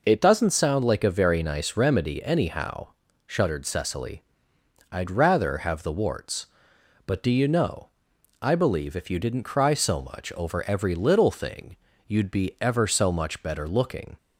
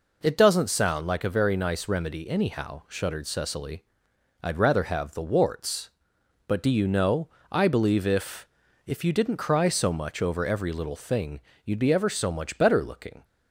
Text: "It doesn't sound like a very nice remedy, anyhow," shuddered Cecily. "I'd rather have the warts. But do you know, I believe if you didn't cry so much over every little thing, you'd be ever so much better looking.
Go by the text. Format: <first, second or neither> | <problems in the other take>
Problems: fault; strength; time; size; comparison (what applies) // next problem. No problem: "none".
first | says "if" twice; at 8.8 s